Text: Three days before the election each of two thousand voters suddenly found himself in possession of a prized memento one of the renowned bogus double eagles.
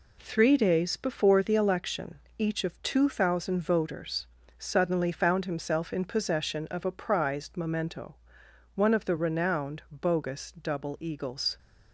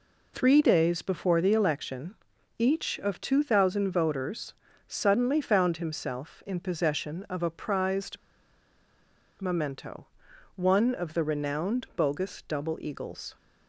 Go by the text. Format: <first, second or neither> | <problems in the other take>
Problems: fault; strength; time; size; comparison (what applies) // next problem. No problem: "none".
first | pauses between "election" and "each"; at 2.1 s; 0.44 s long; slight in the first // pauses between "voters" and "suddenly"; slight; at 4.5 s; 0.36 s long; slight in the first // pauses between "prized" and "memento"; at 8.1 s; 1.2 s long // pauses between "memento" and "one"; noticeable; at 10.0 s; 0.50 s long; noticeable in the first